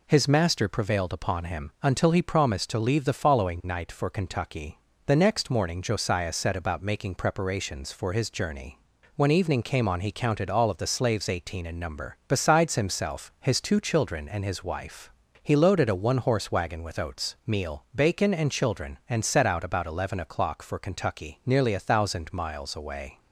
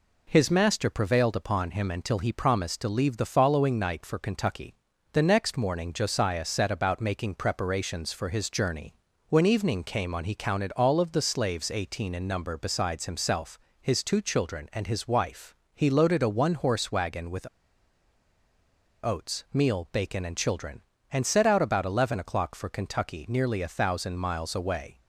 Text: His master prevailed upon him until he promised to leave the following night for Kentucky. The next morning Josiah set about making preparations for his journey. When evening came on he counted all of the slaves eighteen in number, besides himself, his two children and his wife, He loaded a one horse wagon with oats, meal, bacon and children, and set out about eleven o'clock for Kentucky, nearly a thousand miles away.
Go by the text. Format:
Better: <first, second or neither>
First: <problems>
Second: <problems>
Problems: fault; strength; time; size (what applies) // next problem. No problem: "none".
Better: first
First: none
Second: pauses between "with" and "oats"; strong; at 17.4 s; 1.5 s long